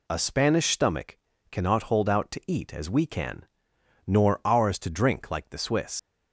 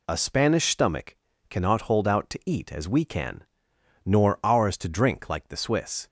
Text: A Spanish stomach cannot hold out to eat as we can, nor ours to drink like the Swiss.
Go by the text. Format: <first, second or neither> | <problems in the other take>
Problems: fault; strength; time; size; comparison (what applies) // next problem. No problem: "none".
second | pauses between "stomach" and "cannot"; slight; at 1.1 s; 0.34 s long; slight in the second // leaves "Swiss" unfinished; at 5.9 s; 90 ms